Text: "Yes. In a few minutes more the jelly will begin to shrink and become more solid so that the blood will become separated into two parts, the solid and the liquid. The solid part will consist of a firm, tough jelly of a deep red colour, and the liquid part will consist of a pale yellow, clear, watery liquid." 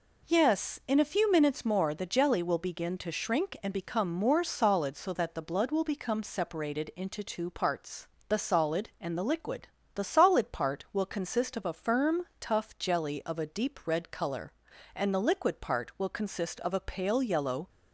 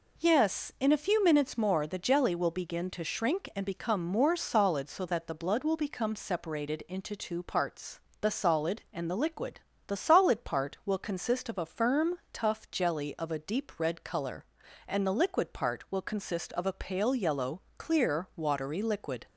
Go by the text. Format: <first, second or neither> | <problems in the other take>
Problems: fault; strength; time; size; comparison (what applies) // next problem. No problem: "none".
second | stops before "clear watery liquid"; at 17.6 s